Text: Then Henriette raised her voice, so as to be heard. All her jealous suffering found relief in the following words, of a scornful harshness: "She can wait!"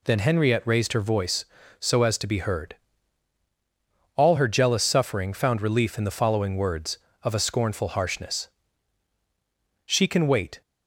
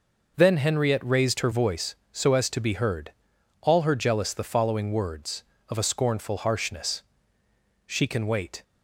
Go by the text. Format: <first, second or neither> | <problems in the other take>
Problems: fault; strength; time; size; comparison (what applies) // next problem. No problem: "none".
first | skips "suffering found relief in"; at 4.3 s